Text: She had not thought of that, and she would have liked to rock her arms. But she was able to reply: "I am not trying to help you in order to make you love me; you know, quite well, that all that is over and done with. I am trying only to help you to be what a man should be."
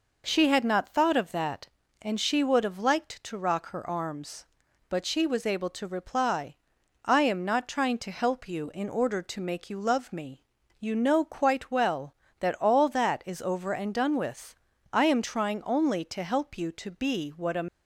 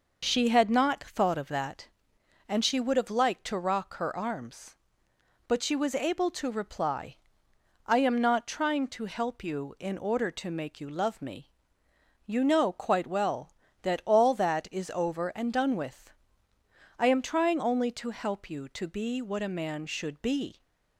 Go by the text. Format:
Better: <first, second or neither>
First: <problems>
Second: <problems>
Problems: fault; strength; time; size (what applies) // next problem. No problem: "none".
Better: second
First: stops before "man should be"; at 17.6 s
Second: none